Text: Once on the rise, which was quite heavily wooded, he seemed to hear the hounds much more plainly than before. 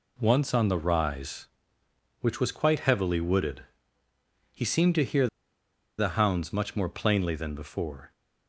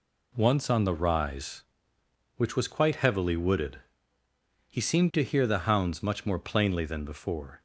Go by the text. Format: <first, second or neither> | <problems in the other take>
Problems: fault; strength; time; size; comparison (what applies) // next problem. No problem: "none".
second | pauses between "hear" and "the"; noticeable; at 5.2 s; 0.72 s long